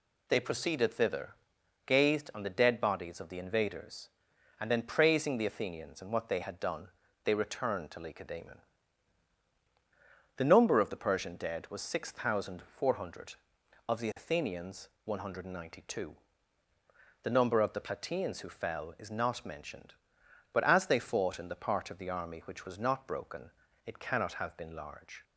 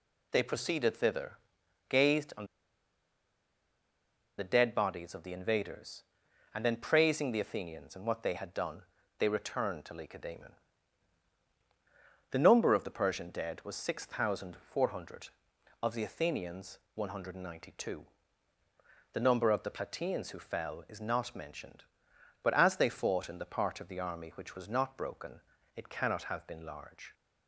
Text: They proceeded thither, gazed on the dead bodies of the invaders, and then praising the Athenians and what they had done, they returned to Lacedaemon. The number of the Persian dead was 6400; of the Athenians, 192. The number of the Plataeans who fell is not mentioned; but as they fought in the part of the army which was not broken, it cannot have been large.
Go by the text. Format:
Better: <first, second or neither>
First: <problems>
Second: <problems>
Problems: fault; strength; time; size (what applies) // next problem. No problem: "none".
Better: first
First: none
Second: pauses between "on" and "the"; strong; at 2.4 s; 1.9 s long